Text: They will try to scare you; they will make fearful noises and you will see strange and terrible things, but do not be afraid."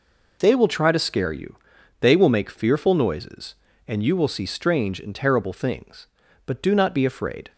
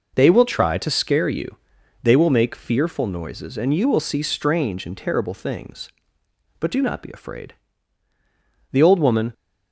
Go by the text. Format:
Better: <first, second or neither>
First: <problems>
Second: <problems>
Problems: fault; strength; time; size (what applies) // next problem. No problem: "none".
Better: first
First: none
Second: goes on to say "The old woman"; from 8.7 s on; 0.60 s long